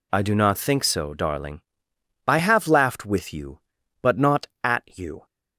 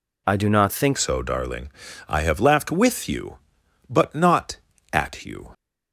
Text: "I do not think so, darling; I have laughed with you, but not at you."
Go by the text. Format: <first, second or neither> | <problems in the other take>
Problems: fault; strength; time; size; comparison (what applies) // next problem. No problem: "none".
first | changes voice at "so"; from 0.9 s on; 4.6 s long